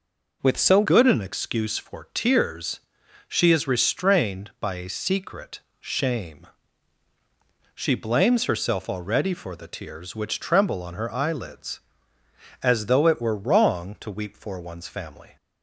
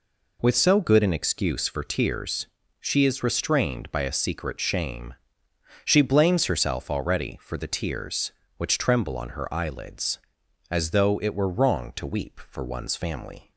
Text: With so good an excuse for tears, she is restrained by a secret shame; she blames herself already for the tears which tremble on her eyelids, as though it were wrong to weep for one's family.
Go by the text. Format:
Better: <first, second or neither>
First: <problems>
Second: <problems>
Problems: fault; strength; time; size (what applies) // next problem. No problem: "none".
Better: second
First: changes voice at "good"; from 0.8 s on; 14.5 s long // pauses between "secret" and "shame"; slight; at 5.5 s; 0.20 s long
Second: none